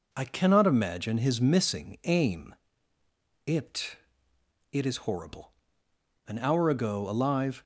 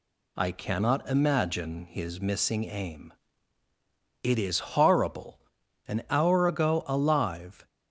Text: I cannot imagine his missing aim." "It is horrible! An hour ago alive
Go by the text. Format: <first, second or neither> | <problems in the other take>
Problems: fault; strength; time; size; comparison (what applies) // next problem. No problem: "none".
second | says "It" twice; at 4.7 s